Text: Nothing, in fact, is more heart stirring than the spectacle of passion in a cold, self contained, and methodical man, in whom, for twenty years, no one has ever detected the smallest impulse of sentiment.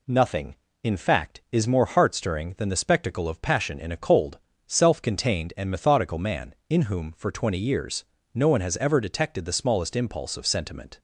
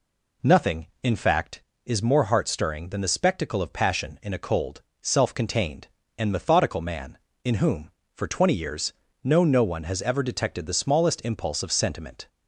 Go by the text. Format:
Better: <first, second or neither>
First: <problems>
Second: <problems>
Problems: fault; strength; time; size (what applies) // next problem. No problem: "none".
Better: first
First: none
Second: says "no" twice; at 9.4 s